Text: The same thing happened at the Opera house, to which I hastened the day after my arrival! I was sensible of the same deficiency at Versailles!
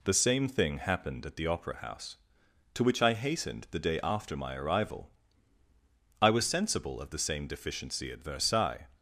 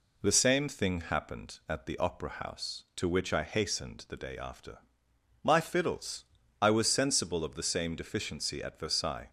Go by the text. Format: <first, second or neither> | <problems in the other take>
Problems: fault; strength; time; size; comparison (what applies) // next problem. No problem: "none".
first | pauses between "after" and "my"; noticeable; at 4.7 s; 0.64 s long // says "fiddles" for "arrival"; at 5.5 s